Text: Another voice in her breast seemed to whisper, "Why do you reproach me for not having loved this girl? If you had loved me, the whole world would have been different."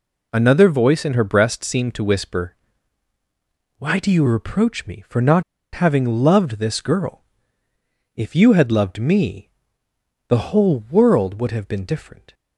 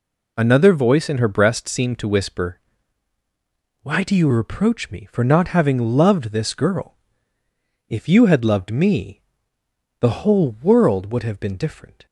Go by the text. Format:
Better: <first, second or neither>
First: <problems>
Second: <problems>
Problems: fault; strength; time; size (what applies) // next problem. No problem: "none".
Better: second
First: pauses between "not" and "having"; slight; at 5.4 s; 0.32 s long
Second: none